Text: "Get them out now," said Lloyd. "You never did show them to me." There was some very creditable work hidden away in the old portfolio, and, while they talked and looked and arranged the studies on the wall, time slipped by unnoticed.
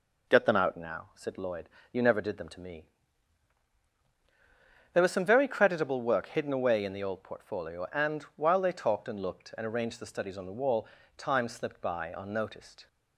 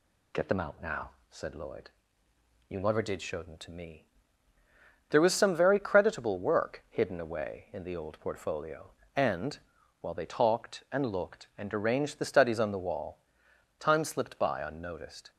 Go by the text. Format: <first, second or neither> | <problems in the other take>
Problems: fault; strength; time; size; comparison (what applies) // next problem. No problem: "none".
second | skips "show"; at 2.3 s